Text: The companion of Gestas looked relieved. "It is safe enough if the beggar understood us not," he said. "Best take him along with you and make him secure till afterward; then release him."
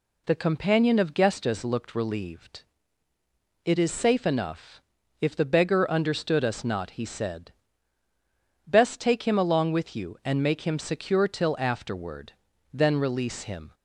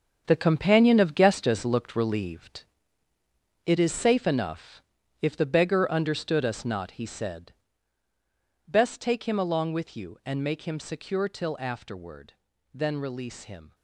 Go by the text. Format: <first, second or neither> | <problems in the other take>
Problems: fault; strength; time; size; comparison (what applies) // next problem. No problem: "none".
first | gets quieter; strong; throughout; 11 dB // pauses between "enough" and "if"; at 4.8 s; 0.40 s long; also in the first